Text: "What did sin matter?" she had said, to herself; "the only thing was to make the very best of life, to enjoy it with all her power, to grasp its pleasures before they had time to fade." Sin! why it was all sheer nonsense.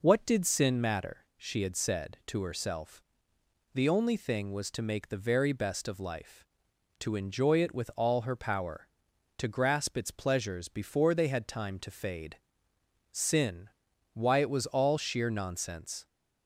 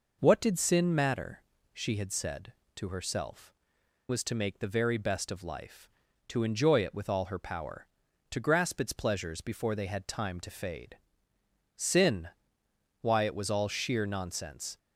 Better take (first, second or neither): first